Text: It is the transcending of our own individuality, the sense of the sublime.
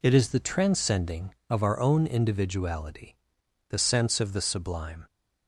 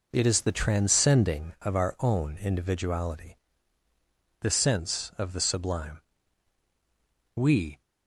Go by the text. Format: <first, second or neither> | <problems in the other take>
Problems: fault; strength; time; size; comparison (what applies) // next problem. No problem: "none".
first | goes on to say "We"; slight; from 7.3 s on; 0.44 s long